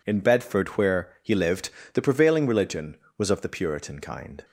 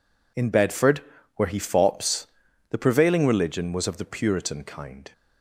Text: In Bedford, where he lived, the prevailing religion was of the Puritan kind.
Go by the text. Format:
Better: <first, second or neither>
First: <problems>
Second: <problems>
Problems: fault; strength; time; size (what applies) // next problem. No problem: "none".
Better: first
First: none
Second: says "fops" for "lived"; at 1.5 s